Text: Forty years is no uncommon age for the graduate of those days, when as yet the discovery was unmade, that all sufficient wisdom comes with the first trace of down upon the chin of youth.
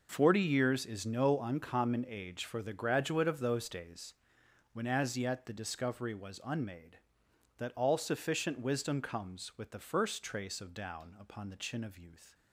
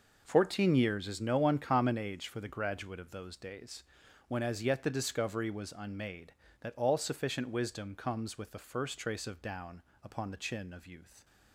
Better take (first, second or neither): first